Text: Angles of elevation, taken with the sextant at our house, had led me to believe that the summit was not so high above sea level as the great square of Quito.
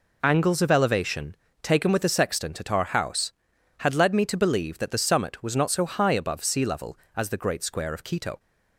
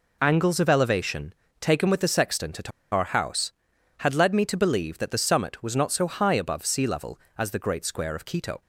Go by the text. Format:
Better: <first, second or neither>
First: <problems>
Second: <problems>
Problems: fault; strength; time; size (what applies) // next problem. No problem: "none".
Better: first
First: none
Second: pauses between "at" and "our"; slight; at 2.7 s; 0.22 s long